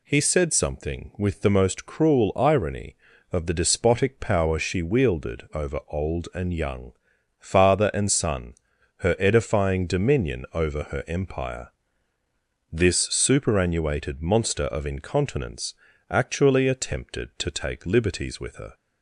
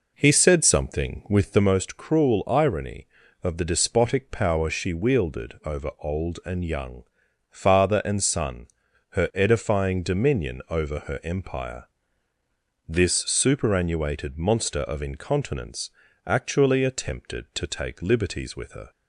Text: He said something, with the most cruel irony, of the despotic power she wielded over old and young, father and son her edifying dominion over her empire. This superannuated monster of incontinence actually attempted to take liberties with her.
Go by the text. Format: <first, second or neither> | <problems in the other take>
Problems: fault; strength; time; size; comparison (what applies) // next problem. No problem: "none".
first | starts louder than the rest; noticeable; until 1.7 s; 4.5 dB // pauses between "son" and "her"; at 8.6 s; 0.42 s long; also in the first // pauses between "incontinence" and "actually"; slight; at 15.9 s; 0.36 s long; slight in the first